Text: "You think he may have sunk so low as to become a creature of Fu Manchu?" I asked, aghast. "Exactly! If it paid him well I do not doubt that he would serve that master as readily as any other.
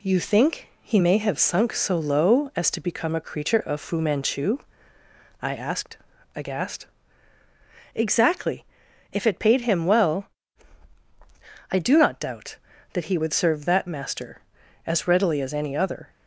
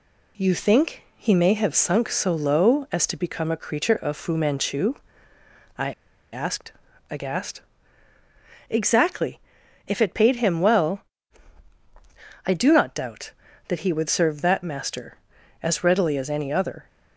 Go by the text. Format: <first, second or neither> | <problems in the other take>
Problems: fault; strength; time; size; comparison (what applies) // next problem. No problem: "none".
first | pauses between "I" and "asked"; at 5.9 s; 0.39 s long // pauses between "well" and "I"; strong; at 11.0 s; 1.4 s long; strong in the first